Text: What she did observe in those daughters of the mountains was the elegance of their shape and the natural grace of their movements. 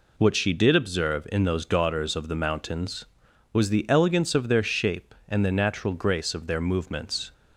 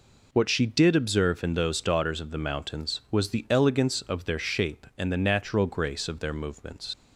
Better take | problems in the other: first | leaves "movements" unfinished; at 6.9 s; 70 ms

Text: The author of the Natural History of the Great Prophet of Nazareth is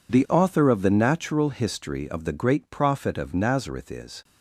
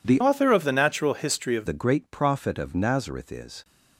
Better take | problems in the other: first | changes voice from "author" to "of"; from 0.2 to 1.6 s; 1.4 s long

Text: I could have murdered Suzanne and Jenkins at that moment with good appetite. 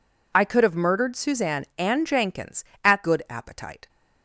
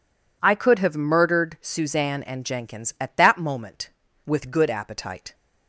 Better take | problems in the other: second | skips "that moment with"; at 3.0 s

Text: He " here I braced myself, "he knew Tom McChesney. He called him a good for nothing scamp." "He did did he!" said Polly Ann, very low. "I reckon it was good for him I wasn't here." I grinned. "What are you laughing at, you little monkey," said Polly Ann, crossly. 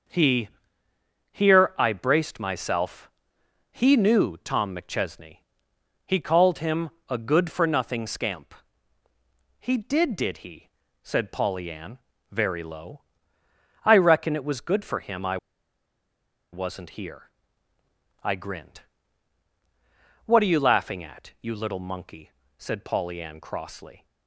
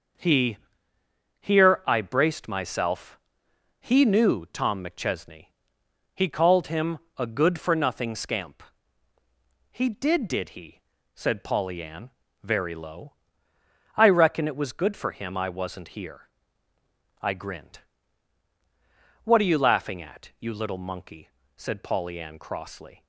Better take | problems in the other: second | pauses between "him" and "a"; slight; at 6.9 s; 0.18 s long; slight in the second // pauses between "I" and "wasn't"; at 15.3 s; 1.1 s long

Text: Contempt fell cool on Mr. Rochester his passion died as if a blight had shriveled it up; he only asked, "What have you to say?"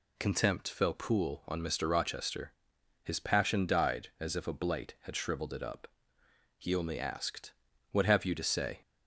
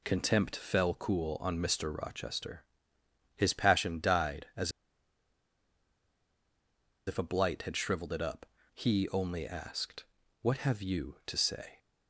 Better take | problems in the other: first | pauses between "Rochester" and "his"; noticeable; at 2.6 s; 0.70 s long; noticeable in the first // pauses between "as" and "if"; strong; at 4.7 s; 2.3 s long

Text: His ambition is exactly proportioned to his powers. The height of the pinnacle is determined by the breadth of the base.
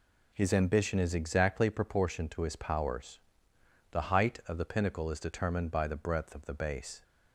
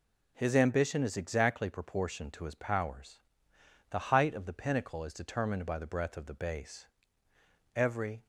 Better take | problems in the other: first | goes on to say "Every"; from 7.7 s on; 0.52 s long

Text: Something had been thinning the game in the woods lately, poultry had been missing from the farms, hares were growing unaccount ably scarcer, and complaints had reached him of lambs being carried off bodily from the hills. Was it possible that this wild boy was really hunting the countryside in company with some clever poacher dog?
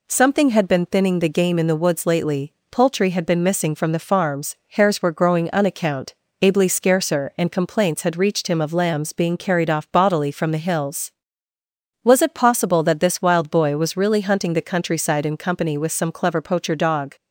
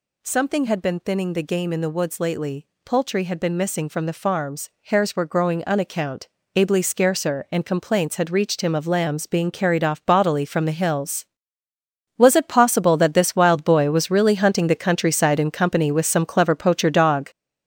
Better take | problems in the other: first | gets louder; strong; throughout; 7.5 dB // pauses between "unaccount" and "ably"; slight; at 6.2 s; 0.28 s long; slight in the first

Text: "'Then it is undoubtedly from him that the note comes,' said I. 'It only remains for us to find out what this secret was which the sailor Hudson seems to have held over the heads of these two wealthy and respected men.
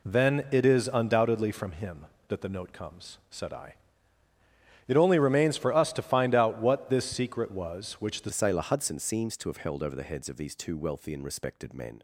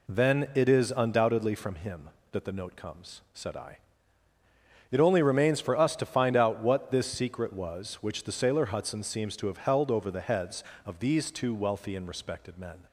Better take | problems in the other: second | changes voice at "sailor"; from 8.3 s on; 3.7 s long

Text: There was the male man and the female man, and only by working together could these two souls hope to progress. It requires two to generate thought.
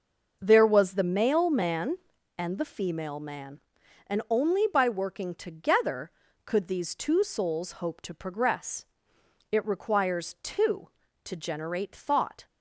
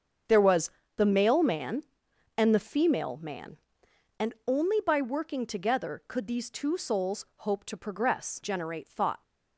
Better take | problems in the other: first | starts louder than the rest; strong; until 1.5 s; 7.5 dB; noticeable in the first // pauses between "was" and "the"; slight; at 0.6 s; 0.26 s long // skips "It requires two to"; at 8.4 s

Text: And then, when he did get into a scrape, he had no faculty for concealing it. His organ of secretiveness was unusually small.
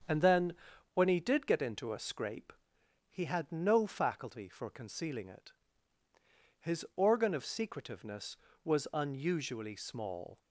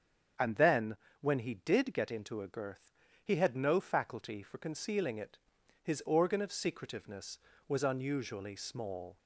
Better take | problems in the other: first | starts louder than the rest; until 1.6 s; 7 dB; also in the first // says "girth" for "scrape"; at 2.4 s

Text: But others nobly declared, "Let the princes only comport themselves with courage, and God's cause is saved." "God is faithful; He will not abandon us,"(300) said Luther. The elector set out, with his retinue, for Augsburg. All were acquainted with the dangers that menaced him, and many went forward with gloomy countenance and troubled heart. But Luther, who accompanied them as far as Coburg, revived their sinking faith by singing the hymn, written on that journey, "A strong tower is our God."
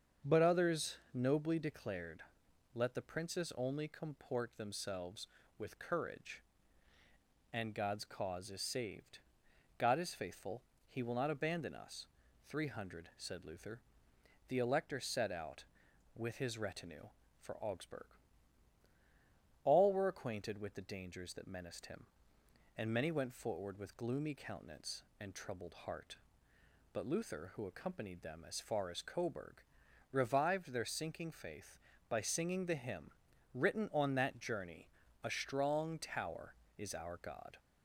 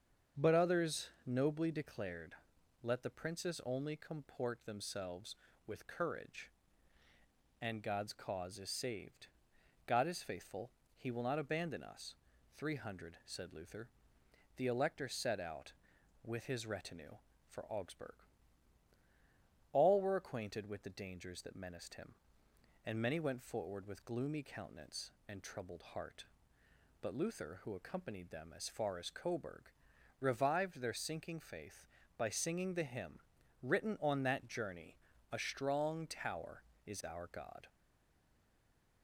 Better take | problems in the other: first | starts louder than the rest; strong; until 1.5 s; 7 dB; strong in the first // pauses between "others" and "nobly"; slight; at 1.1 s; 0.16 s long; slight in the first // stays silent after the last word; noticeable; from 37.6 s on; 1.4 s long

